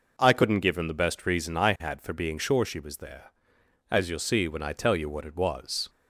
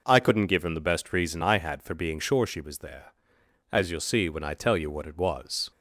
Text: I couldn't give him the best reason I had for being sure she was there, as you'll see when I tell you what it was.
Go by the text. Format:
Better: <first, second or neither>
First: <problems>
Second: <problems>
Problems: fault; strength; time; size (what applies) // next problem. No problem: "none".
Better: neither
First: none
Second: none